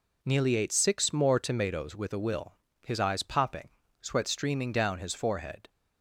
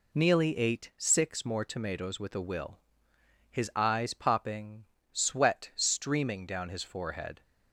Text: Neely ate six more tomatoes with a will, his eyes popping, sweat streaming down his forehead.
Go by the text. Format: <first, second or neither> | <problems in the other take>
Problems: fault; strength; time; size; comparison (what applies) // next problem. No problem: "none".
neither | none